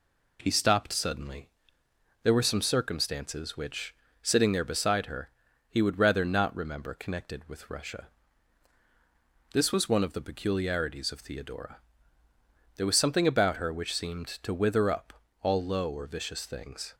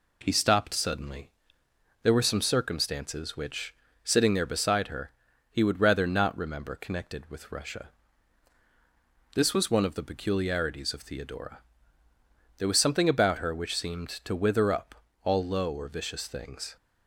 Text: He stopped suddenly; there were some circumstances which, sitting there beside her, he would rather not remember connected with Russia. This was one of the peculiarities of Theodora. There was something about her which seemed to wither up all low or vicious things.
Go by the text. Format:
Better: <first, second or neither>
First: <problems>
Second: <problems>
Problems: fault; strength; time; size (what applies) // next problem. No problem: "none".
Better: neither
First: pauses between "up" and "all"; slight; at 15.1 s; 0.26 s long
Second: pauses between "up" and "all"; slight; at 14.9 s; 0.26 s long